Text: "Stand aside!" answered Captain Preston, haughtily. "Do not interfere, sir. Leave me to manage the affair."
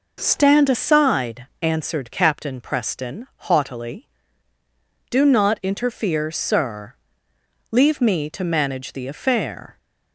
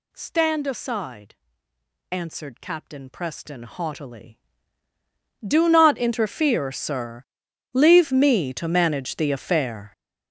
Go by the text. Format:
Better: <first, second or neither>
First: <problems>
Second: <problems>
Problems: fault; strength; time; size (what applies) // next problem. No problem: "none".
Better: first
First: none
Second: gets louder; strong; throughout; 13 dB